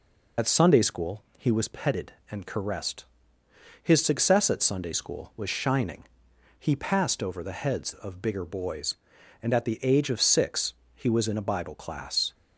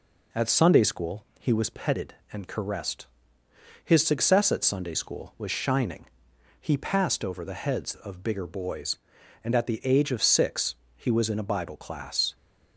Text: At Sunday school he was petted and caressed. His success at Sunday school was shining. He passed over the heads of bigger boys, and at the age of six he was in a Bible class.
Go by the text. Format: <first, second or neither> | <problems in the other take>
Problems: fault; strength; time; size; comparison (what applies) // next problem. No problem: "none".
second | loses the start of "At"; at 0.3 s; 70 ms // pauses between "school" and "he"; slight; at 1.2 s; 0.16 s long; slight in the second // pauses between "six" and "he"; slight; at 10.7 s; 0.20 s long; slight in the second